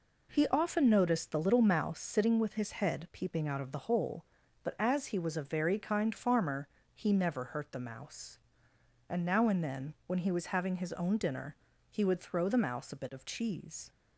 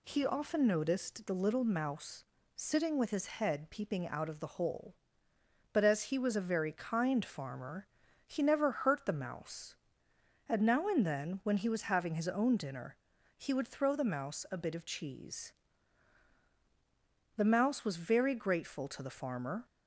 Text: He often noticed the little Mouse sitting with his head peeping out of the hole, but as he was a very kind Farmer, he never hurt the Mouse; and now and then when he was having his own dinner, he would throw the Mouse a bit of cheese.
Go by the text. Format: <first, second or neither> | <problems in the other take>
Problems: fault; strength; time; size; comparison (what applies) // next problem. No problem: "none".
first | pauses between "Mouse" and "sitting"; slight; at 2.2 s; 0.32 s long // goes on to say "The Mouse was very grateful to the Farmer"; strong; from 17.3 s on; 2.3 s long